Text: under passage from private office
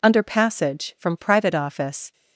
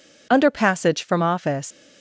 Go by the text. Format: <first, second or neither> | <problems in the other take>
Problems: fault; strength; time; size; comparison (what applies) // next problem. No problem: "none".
first | skips "private"; at 1.2 s